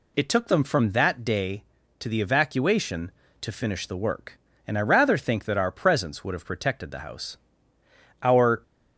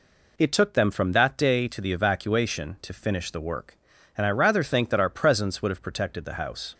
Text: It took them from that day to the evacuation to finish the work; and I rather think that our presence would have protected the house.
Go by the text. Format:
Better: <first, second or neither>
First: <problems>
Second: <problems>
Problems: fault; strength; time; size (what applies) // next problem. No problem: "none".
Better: second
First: goes on to say "Our"; slight; from 8.2 s on; 0.40 s long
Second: none